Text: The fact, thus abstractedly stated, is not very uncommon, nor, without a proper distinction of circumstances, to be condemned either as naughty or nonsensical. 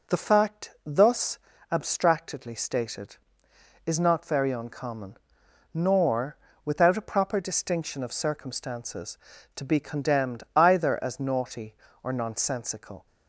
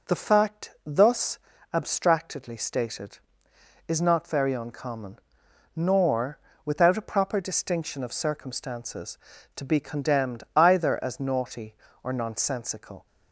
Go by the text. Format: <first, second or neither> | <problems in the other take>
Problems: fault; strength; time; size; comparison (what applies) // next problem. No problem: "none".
neither | pauses between "thus" and "abstractedly"; slight; the same in both